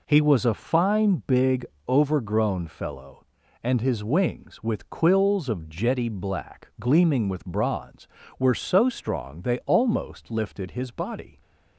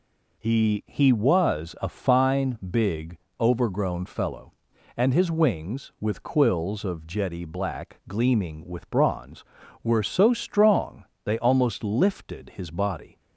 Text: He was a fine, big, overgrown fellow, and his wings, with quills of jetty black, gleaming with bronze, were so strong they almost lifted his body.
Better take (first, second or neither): first